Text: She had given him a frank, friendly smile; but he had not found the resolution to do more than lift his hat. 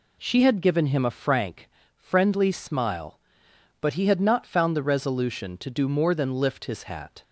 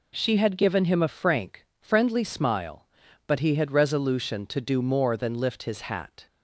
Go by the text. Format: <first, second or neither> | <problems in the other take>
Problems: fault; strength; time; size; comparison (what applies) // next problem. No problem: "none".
first | skips "not found the"; at 3.7 s